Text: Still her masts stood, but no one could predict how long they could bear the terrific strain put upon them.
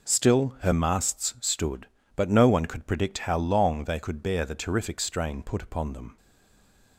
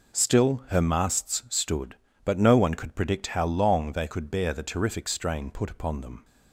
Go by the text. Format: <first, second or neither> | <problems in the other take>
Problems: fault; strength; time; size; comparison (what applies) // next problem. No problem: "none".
second | stays silent after the last word; slight; from 6.1 s on; 0.8 s long